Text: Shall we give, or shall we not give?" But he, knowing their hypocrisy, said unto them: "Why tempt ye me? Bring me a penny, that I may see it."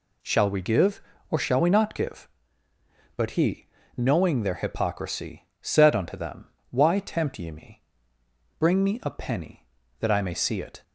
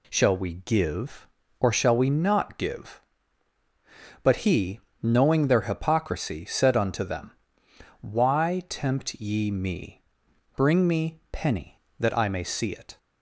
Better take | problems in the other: first | skips "a"; at 11.2 s

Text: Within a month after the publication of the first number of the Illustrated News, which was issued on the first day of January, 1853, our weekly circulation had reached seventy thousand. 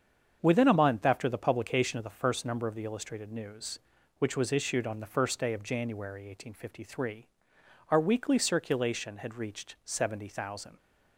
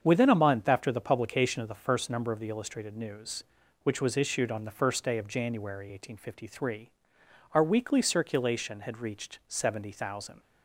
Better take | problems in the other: neither | starts louder than the rest; strong; the same in both

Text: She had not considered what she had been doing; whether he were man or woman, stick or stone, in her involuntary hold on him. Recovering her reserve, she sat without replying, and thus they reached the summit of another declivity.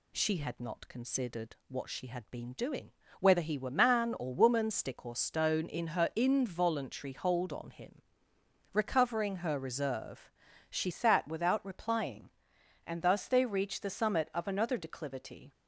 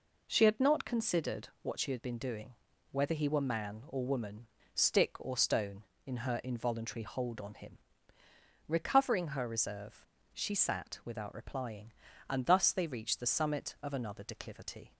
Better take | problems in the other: second | changes voice at "sat"; from 10.9 s on; 4.6 s long

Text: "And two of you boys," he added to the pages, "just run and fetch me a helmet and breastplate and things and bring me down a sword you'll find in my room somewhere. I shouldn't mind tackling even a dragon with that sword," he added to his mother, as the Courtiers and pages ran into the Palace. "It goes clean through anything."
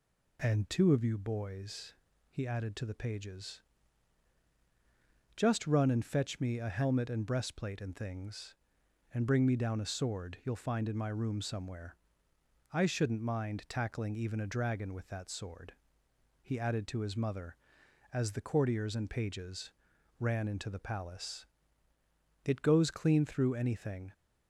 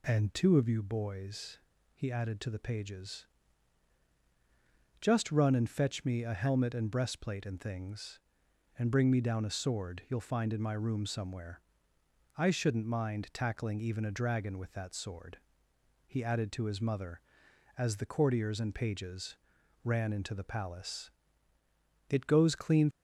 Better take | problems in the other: first | pauses between "pages" and "ran"; noticeable; at 19.3 s; 0.46 s long; noticeable in the first // stops before "through anything"; at 22.9 s

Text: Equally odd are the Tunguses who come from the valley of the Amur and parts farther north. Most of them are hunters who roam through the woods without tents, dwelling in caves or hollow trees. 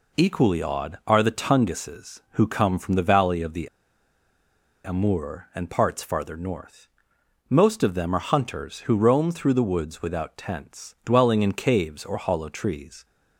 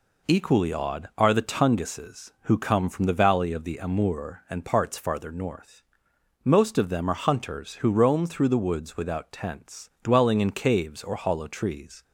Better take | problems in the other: second | pauses between "the" and "Amur"; at 3.6 s; 1.1 s long

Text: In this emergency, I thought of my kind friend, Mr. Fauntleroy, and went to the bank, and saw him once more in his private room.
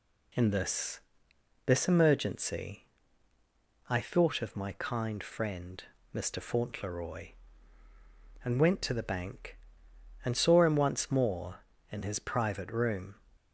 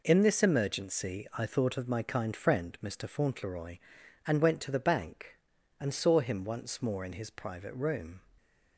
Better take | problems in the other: second | says "this" twice; at 1.6 s

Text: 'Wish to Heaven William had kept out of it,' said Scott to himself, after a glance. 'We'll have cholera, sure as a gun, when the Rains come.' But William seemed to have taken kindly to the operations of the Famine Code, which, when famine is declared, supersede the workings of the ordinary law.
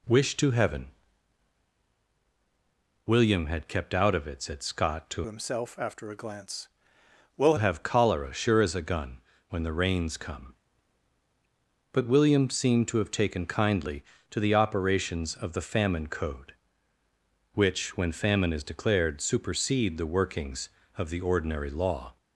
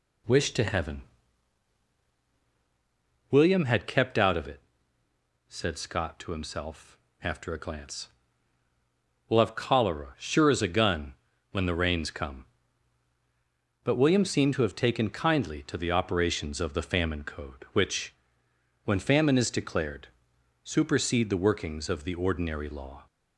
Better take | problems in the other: second | pauses between "Heaven" and "William"; strong; at 0.8 s; 2.1 s long; strong in the second // changes voice from "himself" to "We'll"; from 5.2 to 7.5 s; 2.3 s long

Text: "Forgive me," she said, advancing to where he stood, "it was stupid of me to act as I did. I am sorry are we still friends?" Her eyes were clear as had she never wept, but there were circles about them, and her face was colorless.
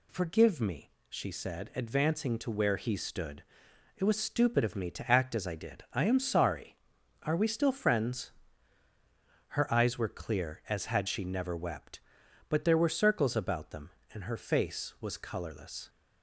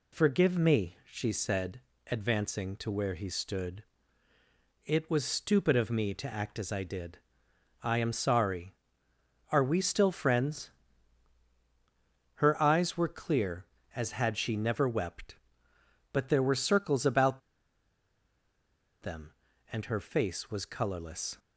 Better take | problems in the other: first | pauses between "about" and "them"; strong; at 17.4 s; 1.6 s long

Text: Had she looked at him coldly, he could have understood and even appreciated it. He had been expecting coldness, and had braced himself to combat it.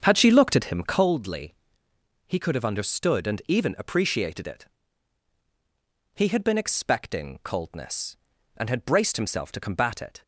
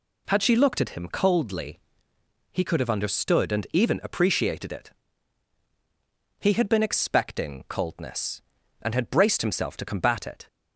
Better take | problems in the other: second | starts louder than the rest; strong; until 1.2 s; 7.5 dB

